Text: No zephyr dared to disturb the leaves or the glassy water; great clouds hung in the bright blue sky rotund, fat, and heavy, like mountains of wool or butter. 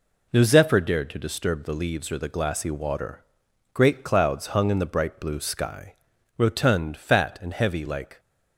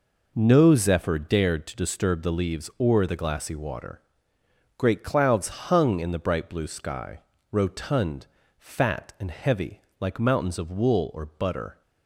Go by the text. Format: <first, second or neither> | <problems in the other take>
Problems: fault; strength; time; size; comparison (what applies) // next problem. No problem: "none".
second | pauses between "sky" and "rotund"; at 5.9 s; 0.42 s long; slight in the second // stops before "mountains of wool or butter"; at 8.1 s